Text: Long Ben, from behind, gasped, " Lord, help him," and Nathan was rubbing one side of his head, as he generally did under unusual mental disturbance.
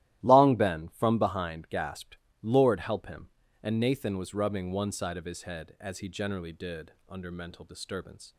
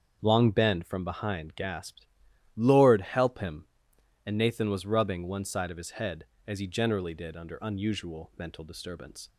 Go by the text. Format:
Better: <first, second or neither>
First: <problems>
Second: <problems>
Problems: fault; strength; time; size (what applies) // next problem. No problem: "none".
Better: second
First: starts louder than the rest; strong; until 1.2 s; 14 dB // pauses between "did" and "under"; slight; at 6.9 s; 0.16 s long // skips "unusual"; at 7.2 s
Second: starts louder than the rest; until 1.2 s; 7 dB